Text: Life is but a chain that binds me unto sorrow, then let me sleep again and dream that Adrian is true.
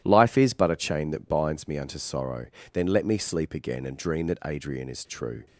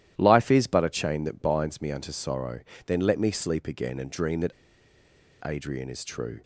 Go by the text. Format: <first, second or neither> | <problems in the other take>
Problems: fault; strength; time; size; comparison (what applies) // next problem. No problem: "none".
first | starts louder than the rest; strong; until 1.1 s; 12 dB; strong in the first // pauses between "that" and "Adrian"; noticeable; at 4.5 s; 0.91 s long